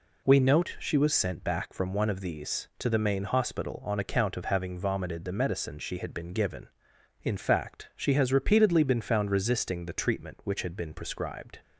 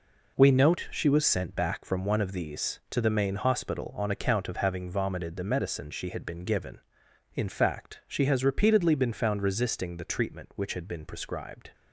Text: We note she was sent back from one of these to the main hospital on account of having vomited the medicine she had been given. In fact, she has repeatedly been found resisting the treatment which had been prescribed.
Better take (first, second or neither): first